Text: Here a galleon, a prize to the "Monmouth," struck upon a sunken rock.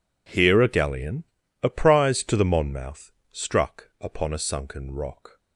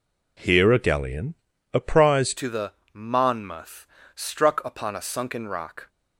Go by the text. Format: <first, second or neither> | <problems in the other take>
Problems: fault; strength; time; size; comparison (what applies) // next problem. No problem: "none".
first | changes voice at "to"; from 2.3 s on; 3.5 s long // pauses between "the" and "Monmouth"; slight; at 2.7 s; 0.20 s long